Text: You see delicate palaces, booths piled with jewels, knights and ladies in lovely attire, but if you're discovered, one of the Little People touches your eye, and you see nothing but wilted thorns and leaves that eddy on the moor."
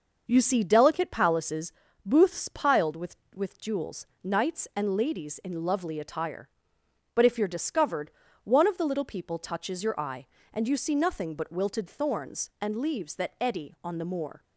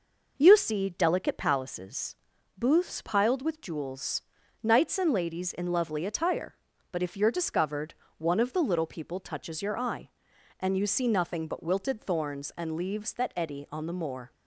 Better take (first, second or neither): second